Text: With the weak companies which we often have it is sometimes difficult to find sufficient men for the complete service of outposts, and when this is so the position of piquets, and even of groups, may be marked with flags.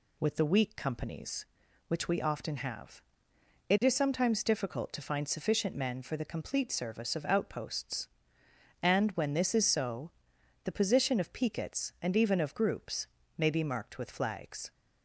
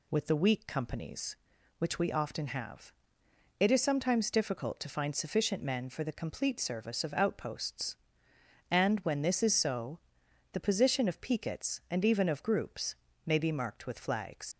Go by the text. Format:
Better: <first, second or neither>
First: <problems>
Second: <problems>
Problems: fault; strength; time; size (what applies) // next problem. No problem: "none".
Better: first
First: pauses between "have" and "it"; noticeable; at 3.0 s; 0.68 s long // pauses between "so" and "the"; noticeable; at 10.1 s; 0.54 s long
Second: pauses between "have" and "it"; noticeable; at 2.9 s; 0.68 s long // pauses between "so" and "the"; noticeable; at 9.9 s; 0.54 s long // leaves "flags" unfinished; at 14.5 s; 75 ms